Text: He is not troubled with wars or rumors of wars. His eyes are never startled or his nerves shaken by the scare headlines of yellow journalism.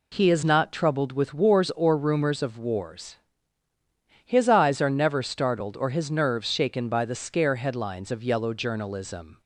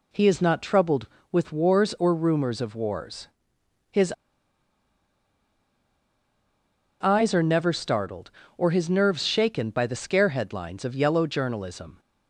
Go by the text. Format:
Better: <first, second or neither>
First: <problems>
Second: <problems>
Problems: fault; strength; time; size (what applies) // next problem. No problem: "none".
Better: first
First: none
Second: pauses between "His" and "eyes"; strong; at 4.1 s; 2.9 s long